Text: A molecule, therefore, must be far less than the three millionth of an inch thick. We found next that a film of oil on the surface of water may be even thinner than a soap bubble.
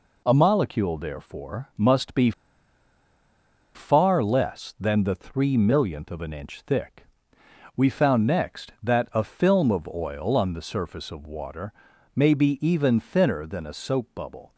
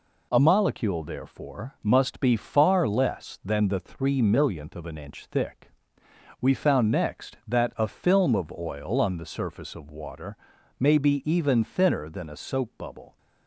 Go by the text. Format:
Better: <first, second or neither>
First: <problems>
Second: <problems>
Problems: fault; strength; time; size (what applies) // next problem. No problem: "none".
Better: second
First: pauses between "be" and "far"; strong; at 2.3 s; 1.4 s long // pauses between "water" and "may"; at 11.7 s; 0.42 s long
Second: pauses between "water" and "may"; at 10.3 s; 0.42 s long